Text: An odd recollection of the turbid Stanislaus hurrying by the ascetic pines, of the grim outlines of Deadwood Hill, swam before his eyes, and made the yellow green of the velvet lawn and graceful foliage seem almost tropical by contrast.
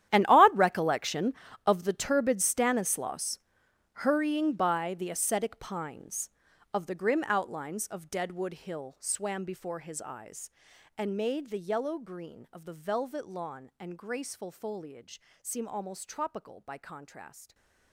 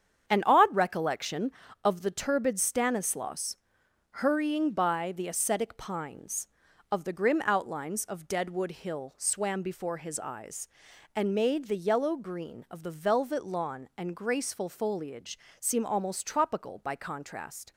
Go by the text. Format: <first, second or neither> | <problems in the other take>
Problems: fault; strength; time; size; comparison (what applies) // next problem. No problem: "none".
second | gets quieter; strong; throughout; 18 dB // starts louder than the rest; strong; until 1.1 s; 11 dB; strong in the second // pauses between "Stanislaus" and "hurrying"; noticeable; at 3.3 s; 0.54 s long; noticeable in the second // pauses between "foliage" and "seem"; slight; at 15.2 s; 0.22 s long; slight in the second